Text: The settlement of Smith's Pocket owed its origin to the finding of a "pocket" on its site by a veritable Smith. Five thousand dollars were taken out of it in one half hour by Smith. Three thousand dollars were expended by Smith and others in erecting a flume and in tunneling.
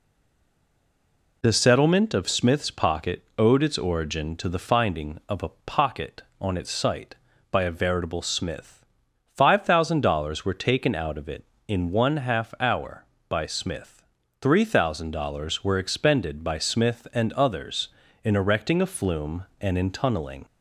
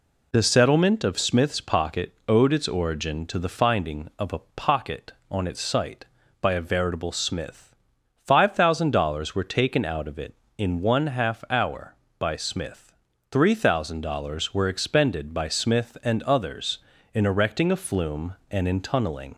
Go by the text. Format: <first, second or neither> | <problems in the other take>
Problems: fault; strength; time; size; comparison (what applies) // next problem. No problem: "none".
second | stays silent before the first word; noticeable; until 1.4 s; 1.4 s long // pauses between "Pocket" and "owed"; slight; at 3.2 s; 0.16 s long; slight in the second